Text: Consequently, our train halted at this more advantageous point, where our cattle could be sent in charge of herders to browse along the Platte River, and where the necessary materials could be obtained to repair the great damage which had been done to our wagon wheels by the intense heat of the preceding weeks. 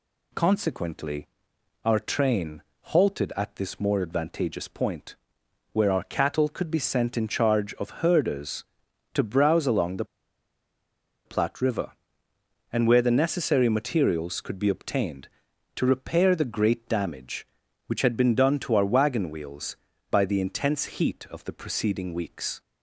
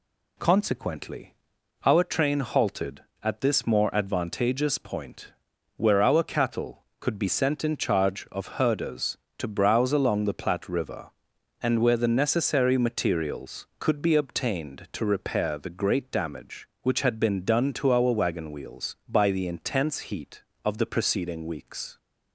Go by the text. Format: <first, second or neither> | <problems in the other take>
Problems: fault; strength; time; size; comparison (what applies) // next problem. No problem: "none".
second | pauses between "train" and "halted"; slight; at 2.6 s; 0.20 s long // pauses between "the" and "Platte"; at 10.0 s; 1.2 s long